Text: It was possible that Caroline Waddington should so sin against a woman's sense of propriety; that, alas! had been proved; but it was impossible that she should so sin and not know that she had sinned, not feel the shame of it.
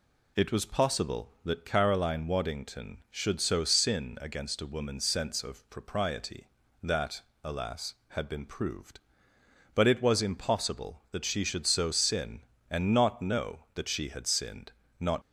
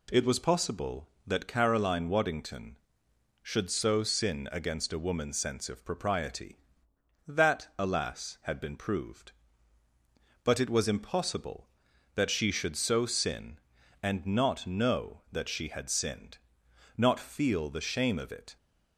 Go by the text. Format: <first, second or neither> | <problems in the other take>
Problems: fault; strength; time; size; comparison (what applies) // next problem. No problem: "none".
second | stops before "feel the shame of it"; at 15.2 s